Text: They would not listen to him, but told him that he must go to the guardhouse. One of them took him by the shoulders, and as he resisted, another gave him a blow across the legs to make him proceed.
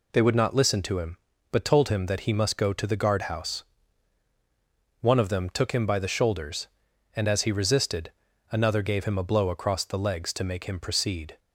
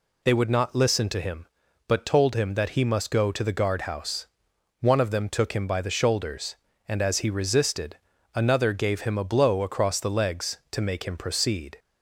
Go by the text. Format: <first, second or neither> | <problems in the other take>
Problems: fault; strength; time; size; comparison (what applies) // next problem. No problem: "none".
neither | none